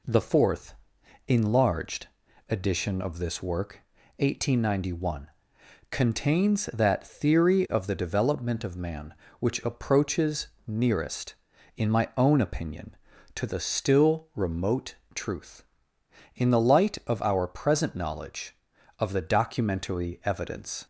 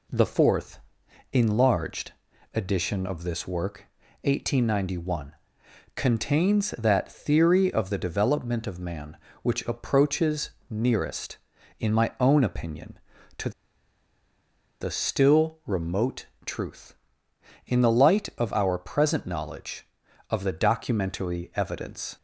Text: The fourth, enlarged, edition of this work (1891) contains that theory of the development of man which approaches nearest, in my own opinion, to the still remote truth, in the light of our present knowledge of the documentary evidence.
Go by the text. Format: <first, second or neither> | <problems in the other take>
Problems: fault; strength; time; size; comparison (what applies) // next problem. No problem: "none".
first | pauses between "approaches" and "nearest"; slight; at 10.4 s; 0.22 s long; slight in the first // pauses between "to" and "the"; strong; at 13.5 s; 1.3 s long // pauses between "remote" and "truth"; slight; at 16.2 s; 0.22 s long; slight in the first